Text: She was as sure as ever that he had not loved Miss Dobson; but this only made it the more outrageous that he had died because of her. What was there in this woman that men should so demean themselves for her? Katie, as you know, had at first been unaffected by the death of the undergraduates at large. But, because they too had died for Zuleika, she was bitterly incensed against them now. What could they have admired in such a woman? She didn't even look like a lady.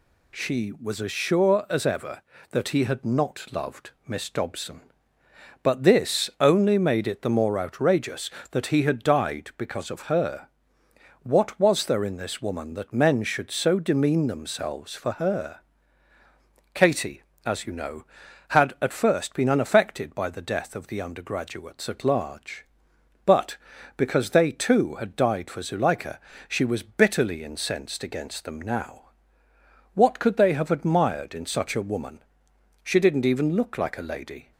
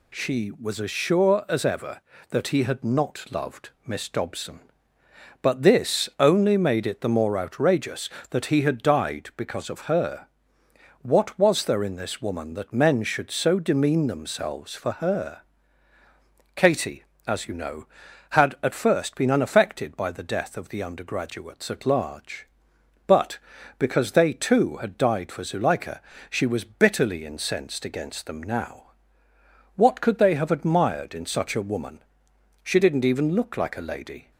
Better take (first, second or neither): neither